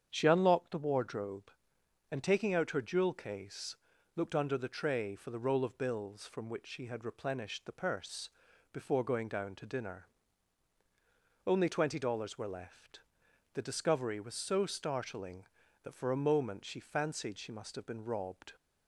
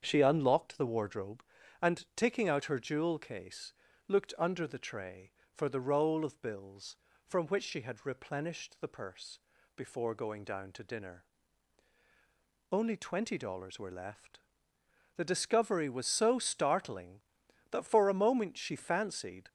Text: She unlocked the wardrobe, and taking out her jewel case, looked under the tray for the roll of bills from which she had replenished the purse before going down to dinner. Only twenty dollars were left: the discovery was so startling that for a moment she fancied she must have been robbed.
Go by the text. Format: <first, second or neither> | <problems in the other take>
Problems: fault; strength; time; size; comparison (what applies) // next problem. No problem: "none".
first | starts louder than the rest; strong; until 1.0 s; 7.5 dB; strong in the first // pauses between "purse" and "before"; at 9.3 s; 0.38 s long; also in the first // stops before "she must have been robbed"; at 19.4 s